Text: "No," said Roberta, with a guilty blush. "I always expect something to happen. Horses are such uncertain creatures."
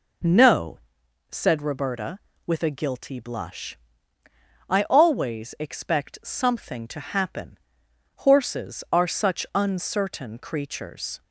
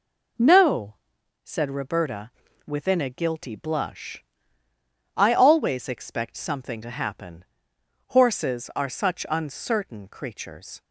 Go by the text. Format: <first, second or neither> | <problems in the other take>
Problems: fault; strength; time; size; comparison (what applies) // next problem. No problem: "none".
first | says "within" for "with"; at 2.6 s